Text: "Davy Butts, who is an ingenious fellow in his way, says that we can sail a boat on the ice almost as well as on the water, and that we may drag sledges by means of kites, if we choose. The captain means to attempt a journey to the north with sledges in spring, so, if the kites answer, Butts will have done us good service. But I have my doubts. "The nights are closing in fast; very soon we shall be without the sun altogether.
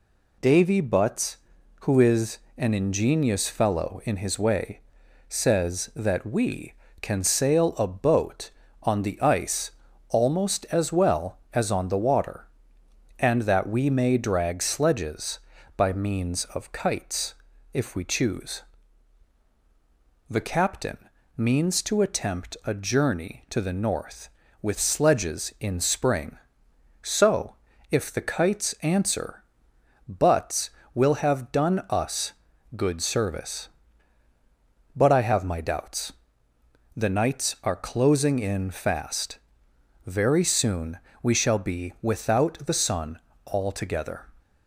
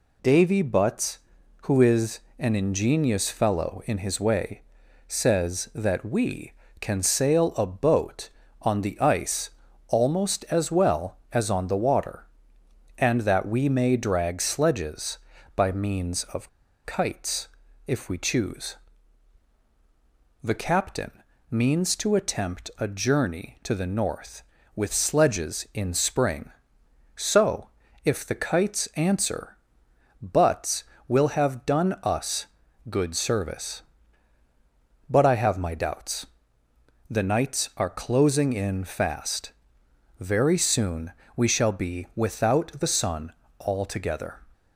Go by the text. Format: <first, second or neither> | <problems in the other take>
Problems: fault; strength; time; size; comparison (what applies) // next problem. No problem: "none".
first | pauses between "is" and "an"; slight; at 2.1 s; 0.18 s long; slight in the first // pauses between "ice" and "almost"; at 9.4 s; 0.38 s long; also in the first // pauses between "of" and "kites"; at 16.4 s; 0.36 s long // pauses between "captain" and "means"; at 21.1 s; 0.40 s long; also in the first // pauses between "us" and "good"; at 32.4 s; 0.42 s long; also in the first // pauses between "soon" and "we"; slight; at 41.1 s; 0.22 s long; slight in the first // pauses between "sun" and "altogether"; slight; at 43.3 s; 0.28 s long; slight in the first